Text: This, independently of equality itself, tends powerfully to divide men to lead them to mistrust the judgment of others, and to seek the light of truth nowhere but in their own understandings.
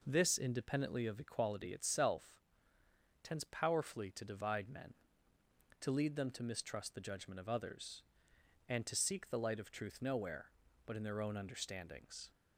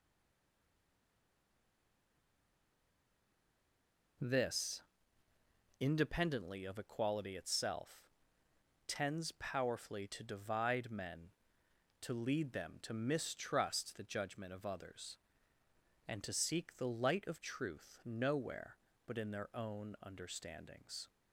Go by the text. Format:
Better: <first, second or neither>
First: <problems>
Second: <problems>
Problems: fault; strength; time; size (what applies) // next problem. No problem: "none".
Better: first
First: none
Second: stays silent before the first word; strong; until 4.1 s; 4.1 s long